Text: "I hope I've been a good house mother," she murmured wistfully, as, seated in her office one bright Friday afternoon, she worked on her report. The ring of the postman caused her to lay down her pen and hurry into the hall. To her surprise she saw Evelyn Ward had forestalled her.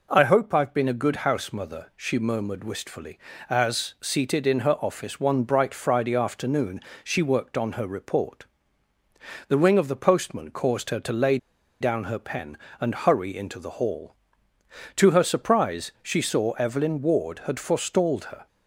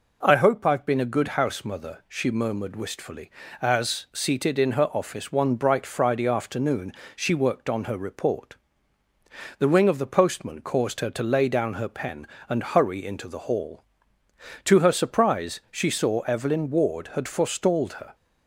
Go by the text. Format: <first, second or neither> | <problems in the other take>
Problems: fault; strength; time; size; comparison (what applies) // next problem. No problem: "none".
second | pauses between "lay" and "down"; at 11.3 s; 0.43 s long